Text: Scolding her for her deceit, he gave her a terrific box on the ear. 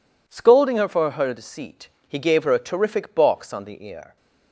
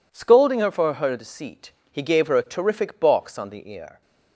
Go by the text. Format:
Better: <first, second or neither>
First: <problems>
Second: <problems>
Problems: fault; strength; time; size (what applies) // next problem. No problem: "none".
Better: neither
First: none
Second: none